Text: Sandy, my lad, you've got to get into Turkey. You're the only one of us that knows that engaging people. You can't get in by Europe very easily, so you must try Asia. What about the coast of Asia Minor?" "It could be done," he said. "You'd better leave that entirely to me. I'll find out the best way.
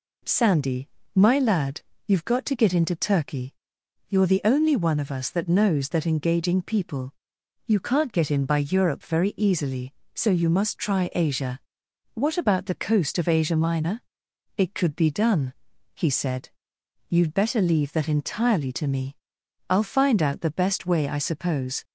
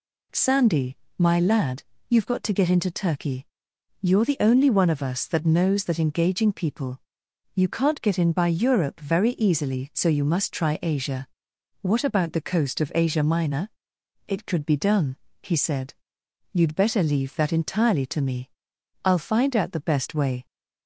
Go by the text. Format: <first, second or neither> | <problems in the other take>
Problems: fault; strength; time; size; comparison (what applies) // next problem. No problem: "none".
second | goes on to say "I suppose"; noticeable; from 21.0 s on; 0.76 s long